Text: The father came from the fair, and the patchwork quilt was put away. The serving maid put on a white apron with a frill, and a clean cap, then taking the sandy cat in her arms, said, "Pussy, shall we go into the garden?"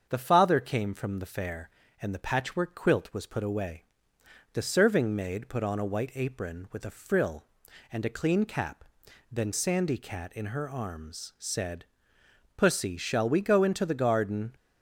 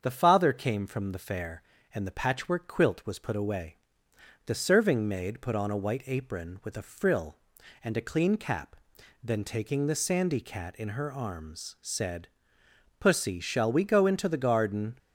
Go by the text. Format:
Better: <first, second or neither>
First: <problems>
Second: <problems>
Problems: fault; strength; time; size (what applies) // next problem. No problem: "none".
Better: second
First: starts louder than the rest; until 1.1 s; 7 dB // skips "taking the"; at 9.5 s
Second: starts louder than the rest; until 1.0 s; 7 dB